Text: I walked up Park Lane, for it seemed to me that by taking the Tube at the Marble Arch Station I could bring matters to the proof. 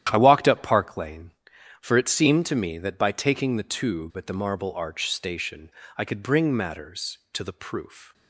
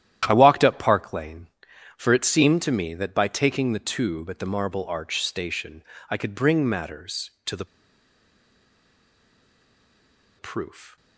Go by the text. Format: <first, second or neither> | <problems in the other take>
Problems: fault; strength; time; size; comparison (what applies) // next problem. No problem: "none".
first | starts louder than the rest; strong; until 1.2 s; 11 dB; strong in the first // pauses between "Station" and "I"; slight; at 5.8 s; 0.28 s long; slight in the first // pauses between "the" and "proof"; strong; at 7.6 s; 2.7 s long